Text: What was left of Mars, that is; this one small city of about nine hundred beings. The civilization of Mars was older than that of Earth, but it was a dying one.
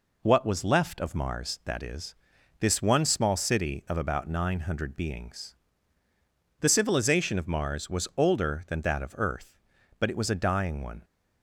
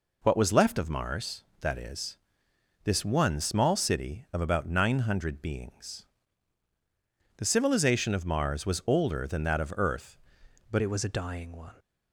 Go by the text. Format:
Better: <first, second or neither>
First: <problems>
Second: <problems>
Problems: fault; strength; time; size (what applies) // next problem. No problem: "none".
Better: first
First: none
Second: changes voice at "it"; from 10.8 s on; 0.9 s long